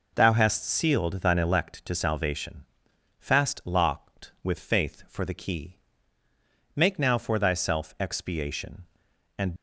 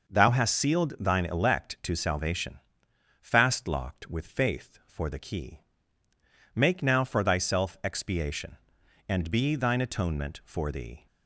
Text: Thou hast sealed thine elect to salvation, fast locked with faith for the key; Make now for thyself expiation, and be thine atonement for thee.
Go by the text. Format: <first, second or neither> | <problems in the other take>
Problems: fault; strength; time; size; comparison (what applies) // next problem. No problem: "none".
second | stops before "be thine atonement for thee"; at 9.5 s